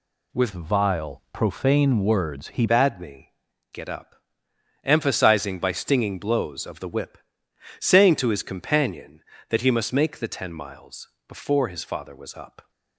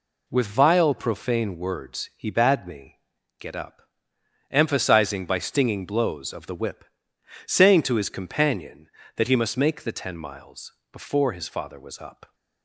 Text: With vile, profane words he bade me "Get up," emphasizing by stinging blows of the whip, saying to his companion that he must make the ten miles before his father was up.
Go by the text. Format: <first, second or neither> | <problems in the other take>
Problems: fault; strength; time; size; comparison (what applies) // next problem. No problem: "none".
second | changes voice from "vile" to "he"; from 0.5 to 2.6 s; 2.1 s long // pauses between "me" and "Get"; at 3.3 s; 0.40 s long; also in the second // pauses between "miles" and "before"; slight; at 11.0 s; 0.20 s long; slight in the second